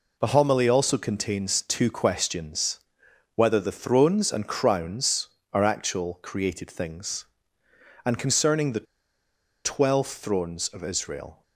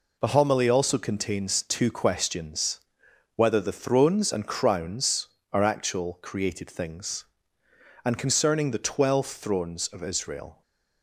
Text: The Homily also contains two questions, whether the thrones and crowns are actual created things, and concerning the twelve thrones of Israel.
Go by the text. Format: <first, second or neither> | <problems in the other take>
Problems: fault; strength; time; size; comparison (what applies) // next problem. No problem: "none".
second | pauses between "the" and "twelve"; noticeable; at 8.8 s; 0.80 s long